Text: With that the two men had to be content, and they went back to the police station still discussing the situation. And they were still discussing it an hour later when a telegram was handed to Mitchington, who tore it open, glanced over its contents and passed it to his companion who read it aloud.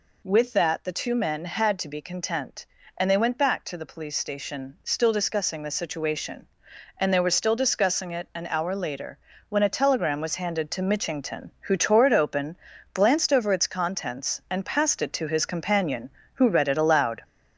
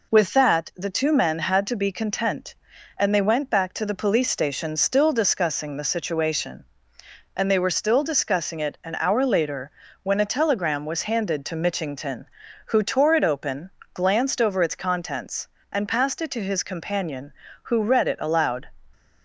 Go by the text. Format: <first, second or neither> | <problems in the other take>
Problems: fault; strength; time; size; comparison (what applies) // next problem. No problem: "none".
second | gets louder; noticeable; throughout; 4 dB // pauses between "later" and "when"; slight; at 9.1 s; 0.30 s long; slight in the second